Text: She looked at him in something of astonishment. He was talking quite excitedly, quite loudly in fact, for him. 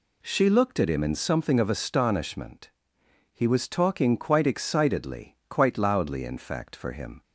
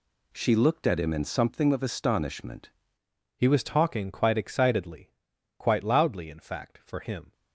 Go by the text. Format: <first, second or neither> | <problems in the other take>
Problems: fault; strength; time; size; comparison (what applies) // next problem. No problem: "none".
first | changes voice at "He"; from 3.3 s on; 4.0 s long